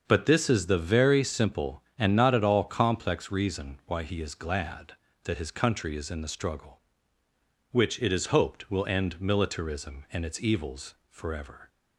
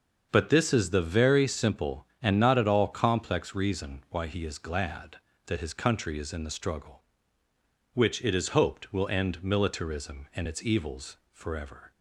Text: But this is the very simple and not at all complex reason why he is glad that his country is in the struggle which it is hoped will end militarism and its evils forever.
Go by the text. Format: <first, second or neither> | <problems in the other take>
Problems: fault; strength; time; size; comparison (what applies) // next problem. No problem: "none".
neither | starts louder than the rest; the same in both